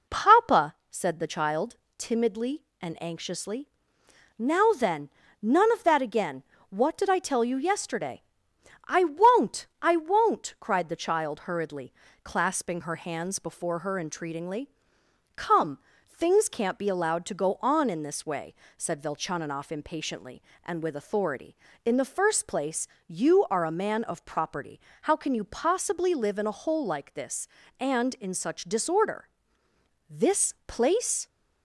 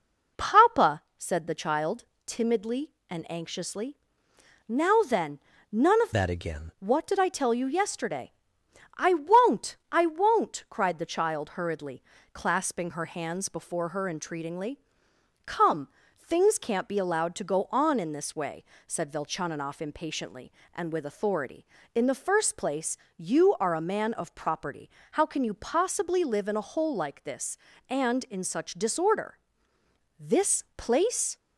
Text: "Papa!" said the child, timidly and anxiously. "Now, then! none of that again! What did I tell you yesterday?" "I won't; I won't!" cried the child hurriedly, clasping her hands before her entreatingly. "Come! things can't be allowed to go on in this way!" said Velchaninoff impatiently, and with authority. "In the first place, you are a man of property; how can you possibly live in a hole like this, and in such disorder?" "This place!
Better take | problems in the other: first | changes voice from "that" to "again"; from 6.1 to 6.7 s; 0.6 s long

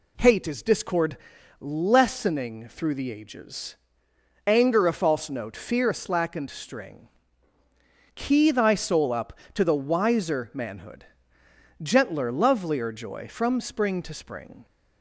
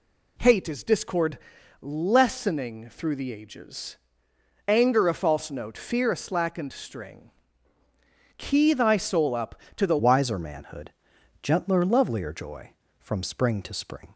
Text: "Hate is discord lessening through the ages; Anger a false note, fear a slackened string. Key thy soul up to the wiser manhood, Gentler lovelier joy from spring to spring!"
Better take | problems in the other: first | pauses between "discord" and "lessening"; at 1.3 s; 0.44 s long; also in the first // changes voice at "wiser"; from 9.9 s on; 4.2 s long

